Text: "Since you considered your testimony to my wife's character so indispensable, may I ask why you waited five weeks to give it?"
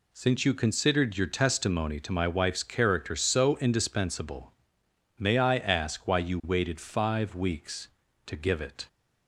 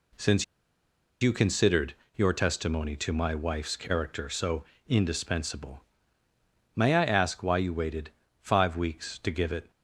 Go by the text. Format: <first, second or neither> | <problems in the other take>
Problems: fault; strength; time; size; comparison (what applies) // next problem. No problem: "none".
first | pauses between "Since" and "you"; noticeable; at 0.4 s; 0.77 s long // pauses between "considered" and "your"; slight; at 1.9 s; 0.22 s long // pauses between "so" and "indispensable"; slight; at 4.6 s; 0.24 s long // pauses between "waited" and "five"; slight; at 8.1 s; 0.30 s long